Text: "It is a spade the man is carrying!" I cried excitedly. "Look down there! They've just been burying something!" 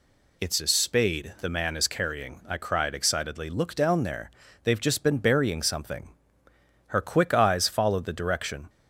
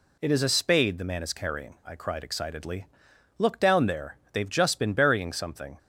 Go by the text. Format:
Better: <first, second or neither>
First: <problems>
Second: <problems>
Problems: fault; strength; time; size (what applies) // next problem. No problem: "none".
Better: second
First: goes on to say "Her quick eyes followed the direction"; strong; from 6.8 s on; 1.8 s long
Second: none